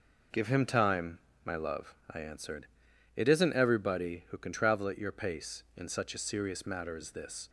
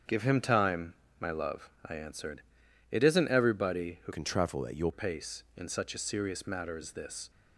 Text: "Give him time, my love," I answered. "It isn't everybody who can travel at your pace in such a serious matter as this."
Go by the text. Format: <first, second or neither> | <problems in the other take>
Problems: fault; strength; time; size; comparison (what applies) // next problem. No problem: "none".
first | starts louder than the rest; strong; until 1.3 s; 7.5 dB // changes voice from "can" to "your"; from 4.1 to 4.9 s; 0.8 s long